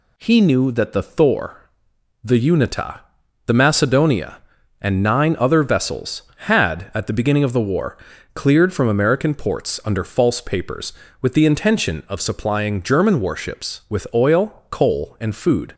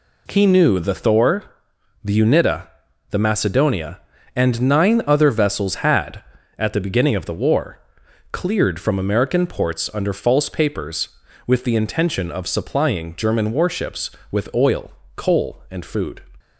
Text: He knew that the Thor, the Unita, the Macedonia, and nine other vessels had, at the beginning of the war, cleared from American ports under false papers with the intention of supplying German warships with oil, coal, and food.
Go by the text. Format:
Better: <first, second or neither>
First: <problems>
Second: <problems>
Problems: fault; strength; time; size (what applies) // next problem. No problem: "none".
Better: first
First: none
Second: skips "that"; at 0.7 s